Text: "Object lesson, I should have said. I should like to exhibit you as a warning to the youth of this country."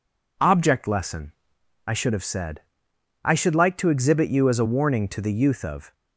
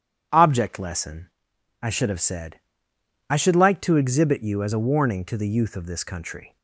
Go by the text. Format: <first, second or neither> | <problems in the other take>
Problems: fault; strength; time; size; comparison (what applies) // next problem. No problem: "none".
second | stops before "this country"; at 5.9 s